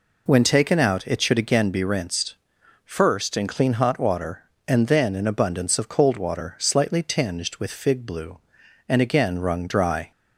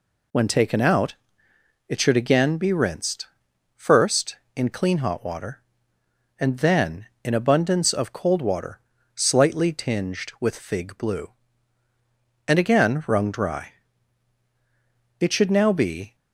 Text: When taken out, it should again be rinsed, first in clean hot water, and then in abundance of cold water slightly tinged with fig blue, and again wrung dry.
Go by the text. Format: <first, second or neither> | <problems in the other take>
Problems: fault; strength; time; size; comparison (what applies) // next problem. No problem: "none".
first | pauses between "water" and "slightly"; slight; at 8.7 s; 0.34 s long // goes on to say "It should now be"; noticeable; from 15.1 s on; 0.96 s long